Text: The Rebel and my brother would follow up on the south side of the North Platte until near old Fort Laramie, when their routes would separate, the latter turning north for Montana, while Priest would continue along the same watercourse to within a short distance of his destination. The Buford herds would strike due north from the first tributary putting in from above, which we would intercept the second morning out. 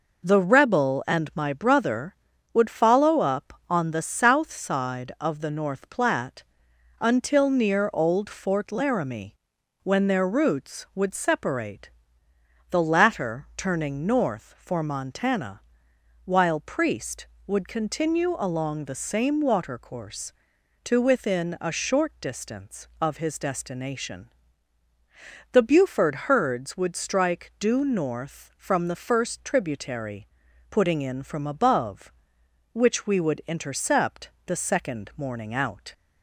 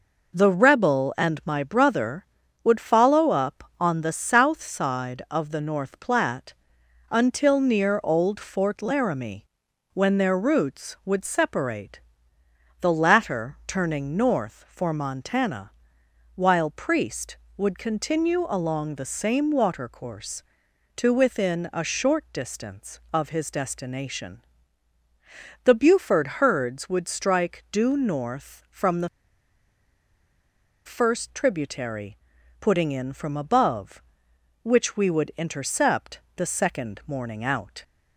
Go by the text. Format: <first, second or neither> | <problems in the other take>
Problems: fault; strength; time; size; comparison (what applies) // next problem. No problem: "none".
first | pauses between "Platte" and "until"; noticeable; at 6.5 s; 0.54 s long; noticeable in the first // pauses between "the" and "first"; strong; at 29.0 s; 1.7 s long // pauses between "tributary" and "putting"; noticeable; at 32.1 s; 0.46 s long; noticeable in the first // pauses between "intercept" and "the"; slight; at 36.2 s; 0.16 s long; slight in the first